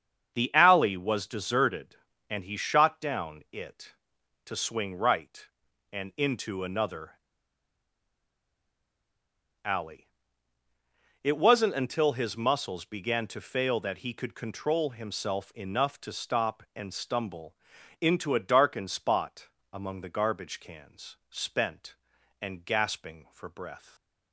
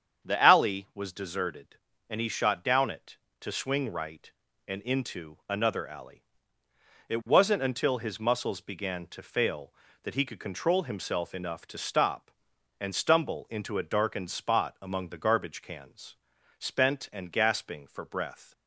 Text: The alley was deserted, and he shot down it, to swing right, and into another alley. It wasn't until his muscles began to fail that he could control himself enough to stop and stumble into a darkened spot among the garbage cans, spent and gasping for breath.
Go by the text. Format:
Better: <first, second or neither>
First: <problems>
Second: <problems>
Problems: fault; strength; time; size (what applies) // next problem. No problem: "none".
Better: second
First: starts louder than the rest; strong; until 1.3 s; 7 dB // pauses between "another" and "alley"; strong; at 7.1 s; 2.5 s long // pauses between "stumble" and "into"; noticeable; at 17.5 s; 0.46 s long // pauses between "spot" and "among"; slight; at 19.4 s; 0.26 s long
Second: starts louder than the rest; strong; until 1.3 s; 8 dB